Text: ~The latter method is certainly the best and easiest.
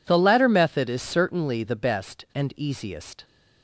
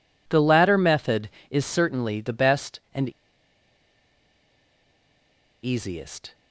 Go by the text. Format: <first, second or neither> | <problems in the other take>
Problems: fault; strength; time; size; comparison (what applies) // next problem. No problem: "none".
first | pauses between "and" and "easiest"; strong; at 3.1 s; 2.5 s long